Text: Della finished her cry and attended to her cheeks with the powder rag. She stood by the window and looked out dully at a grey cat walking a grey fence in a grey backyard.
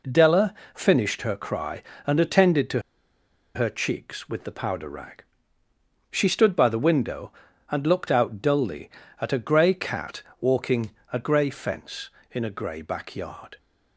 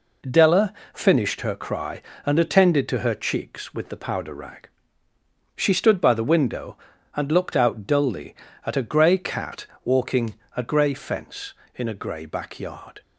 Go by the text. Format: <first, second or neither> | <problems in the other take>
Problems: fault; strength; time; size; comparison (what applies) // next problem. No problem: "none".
second | pauses between "Della" and "finished"; slight; at 0.5 s; 0.20 s long; slight in the second // pauses between "to" and "her"; noticeable; at 2.8 s; 0.74 s long // pauses between "cat" and "walking"; slight; at 10.2 s; 0.18 s long; slight in the second // pauses between "walking" and "a"; slight; at 10.8 s; 0.22 s long; slight in the second